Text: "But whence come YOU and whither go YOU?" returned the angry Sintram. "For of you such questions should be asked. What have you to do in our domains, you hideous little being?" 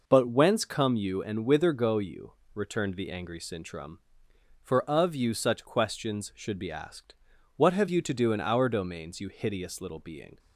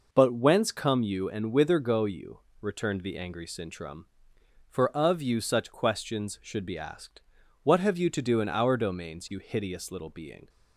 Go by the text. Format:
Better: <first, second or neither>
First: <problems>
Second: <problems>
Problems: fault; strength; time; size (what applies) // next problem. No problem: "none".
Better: neither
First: none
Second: none